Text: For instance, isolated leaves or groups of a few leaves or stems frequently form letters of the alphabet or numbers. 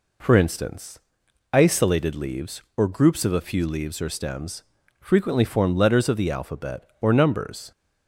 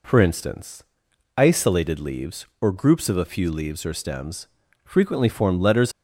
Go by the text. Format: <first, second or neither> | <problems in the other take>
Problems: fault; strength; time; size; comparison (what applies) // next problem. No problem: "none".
first | pauses between "stems" and "frequently"; at 4.4 s; 0.38 s long; also in the first // stops before "of the alphabet or numbers"; at 5.9 s